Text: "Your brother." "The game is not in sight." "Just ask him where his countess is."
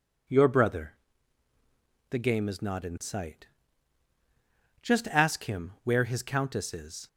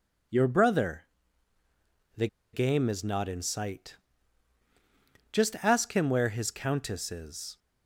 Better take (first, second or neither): first